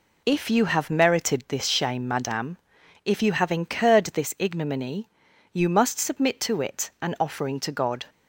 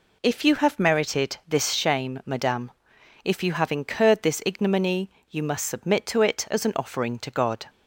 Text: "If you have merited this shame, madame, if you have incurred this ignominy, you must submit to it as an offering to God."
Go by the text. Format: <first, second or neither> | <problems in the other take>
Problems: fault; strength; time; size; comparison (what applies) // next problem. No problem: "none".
second | skips "as"; at 6.9 s